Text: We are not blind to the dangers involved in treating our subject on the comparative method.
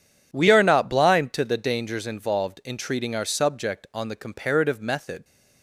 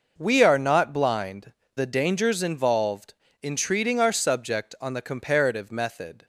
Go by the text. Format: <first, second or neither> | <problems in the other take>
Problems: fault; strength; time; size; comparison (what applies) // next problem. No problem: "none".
first | skips "to"; at 1.6 s